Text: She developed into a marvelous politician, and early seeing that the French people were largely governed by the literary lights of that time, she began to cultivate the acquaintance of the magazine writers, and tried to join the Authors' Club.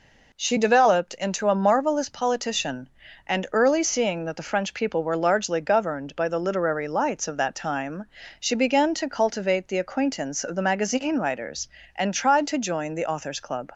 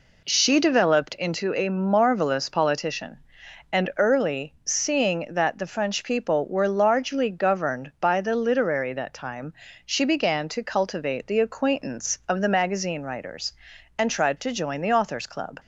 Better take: first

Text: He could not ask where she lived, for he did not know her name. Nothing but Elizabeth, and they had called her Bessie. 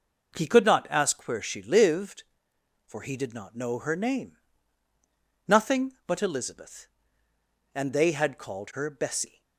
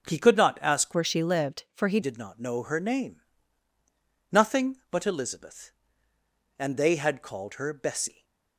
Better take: first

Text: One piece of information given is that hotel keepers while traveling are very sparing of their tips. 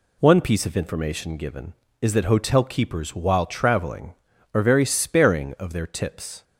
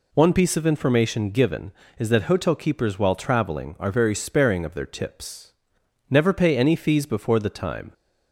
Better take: first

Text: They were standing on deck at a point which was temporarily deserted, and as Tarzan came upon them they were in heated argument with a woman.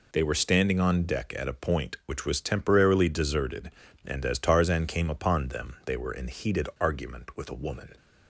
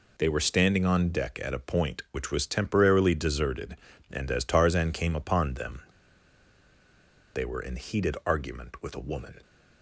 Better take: first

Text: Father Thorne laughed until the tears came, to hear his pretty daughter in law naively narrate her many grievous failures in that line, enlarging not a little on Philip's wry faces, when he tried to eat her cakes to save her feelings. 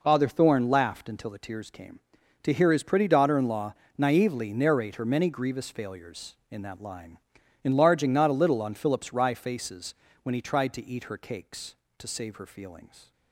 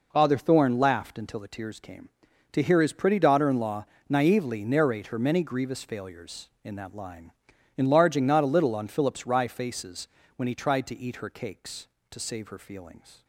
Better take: neither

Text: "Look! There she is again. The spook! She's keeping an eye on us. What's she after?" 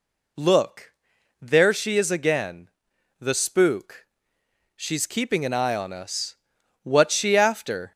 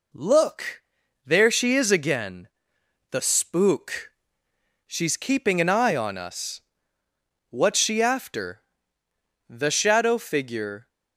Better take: first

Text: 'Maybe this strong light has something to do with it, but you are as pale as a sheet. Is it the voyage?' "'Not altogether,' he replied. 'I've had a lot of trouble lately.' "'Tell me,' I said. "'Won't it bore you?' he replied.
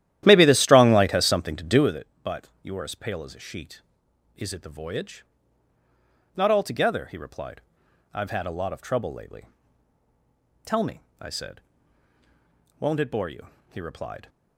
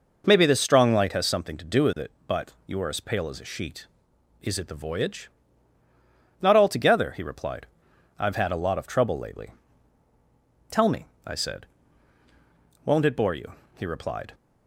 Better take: second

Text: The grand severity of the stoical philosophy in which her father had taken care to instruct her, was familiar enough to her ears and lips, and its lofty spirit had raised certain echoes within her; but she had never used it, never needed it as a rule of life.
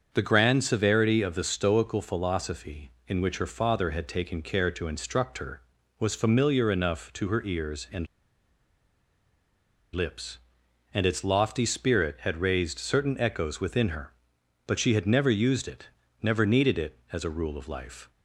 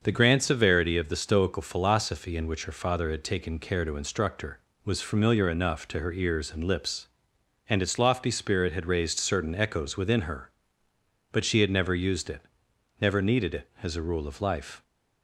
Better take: second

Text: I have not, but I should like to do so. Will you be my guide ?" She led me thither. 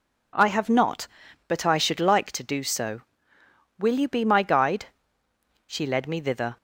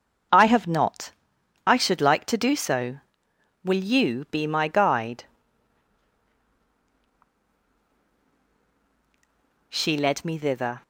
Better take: first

